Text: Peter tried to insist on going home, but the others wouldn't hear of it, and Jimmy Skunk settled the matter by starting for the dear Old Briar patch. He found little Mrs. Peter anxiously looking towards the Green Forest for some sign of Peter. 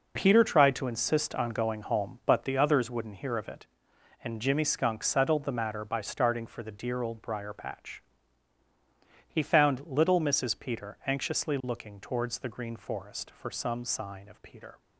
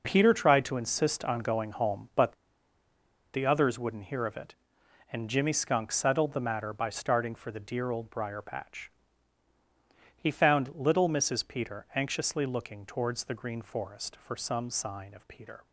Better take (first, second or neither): first